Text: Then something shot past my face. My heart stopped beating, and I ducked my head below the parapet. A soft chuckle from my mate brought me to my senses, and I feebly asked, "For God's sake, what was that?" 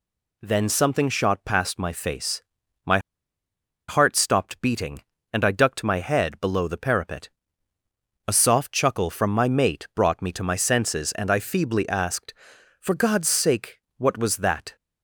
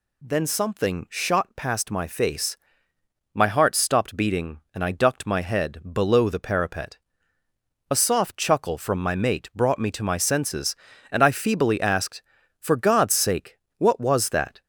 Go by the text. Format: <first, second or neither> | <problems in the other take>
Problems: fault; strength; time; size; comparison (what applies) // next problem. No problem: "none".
second | pauses between "My" and "heart"; noticeable; at 2.9 s; 0.90 s long